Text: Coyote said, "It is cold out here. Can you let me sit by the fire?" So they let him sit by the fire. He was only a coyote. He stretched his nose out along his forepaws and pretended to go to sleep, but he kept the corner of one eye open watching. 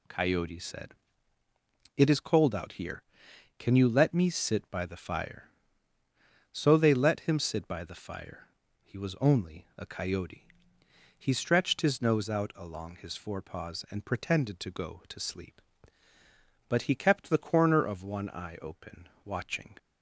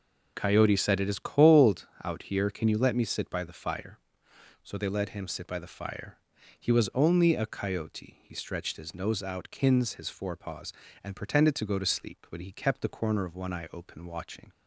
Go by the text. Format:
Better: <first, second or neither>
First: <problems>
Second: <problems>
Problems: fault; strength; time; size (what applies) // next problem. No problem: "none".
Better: first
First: none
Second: pauses between "cold" and "out"; slight; at 1.8 s; 0.16 s long // says "kins" for "along"; at 9.5 s